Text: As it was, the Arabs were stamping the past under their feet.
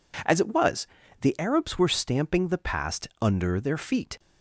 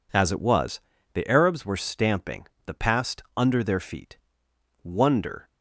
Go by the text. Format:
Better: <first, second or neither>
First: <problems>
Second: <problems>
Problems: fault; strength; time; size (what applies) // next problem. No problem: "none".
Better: first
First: none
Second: pauses between "stamping" and "the"; slight; at 2.4 s; 0.20 s long // goes on to say "Wonder"; noticeable; from 4.8 s on; 0.68 s long